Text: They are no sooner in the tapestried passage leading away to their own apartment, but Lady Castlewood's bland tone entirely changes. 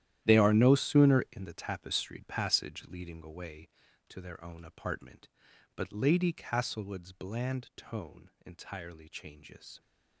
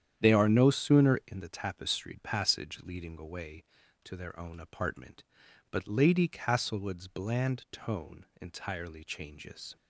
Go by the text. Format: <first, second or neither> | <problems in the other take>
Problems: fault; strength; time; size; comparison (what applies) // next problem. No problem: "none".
second | gets quieter; strong; throughout; 14.5 dB // starts louder than the rest; strong; until 1.2 s; 12 dB; strong in the second